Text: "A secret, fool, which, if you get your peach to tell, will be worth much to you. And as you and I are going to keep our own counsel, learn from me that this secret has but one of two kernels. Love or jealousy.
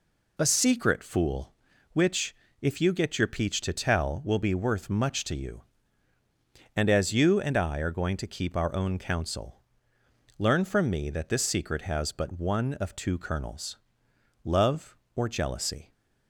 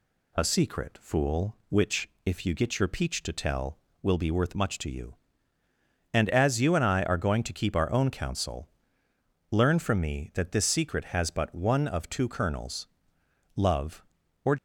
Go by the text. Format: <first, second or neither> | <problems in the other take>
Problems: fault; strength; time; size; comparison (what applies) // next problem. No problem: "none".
first | stops before "jealousy"; at 14.5 s